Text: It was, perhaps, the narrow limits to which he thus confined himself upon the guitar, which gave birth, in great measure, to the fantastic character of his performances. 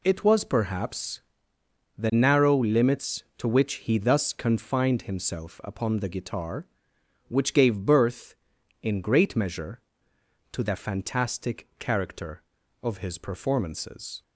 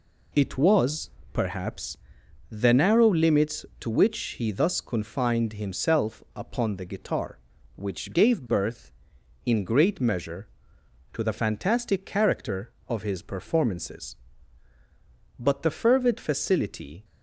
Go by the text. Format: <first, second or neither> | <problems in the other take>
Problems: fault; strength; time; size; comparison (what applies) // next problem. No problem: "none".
first | pauses between "which" and "he"; slight; at 4.1 s; 0.20 s long // goes on to say "But the fervid facility"; from 15.3 s on; 1.6 s long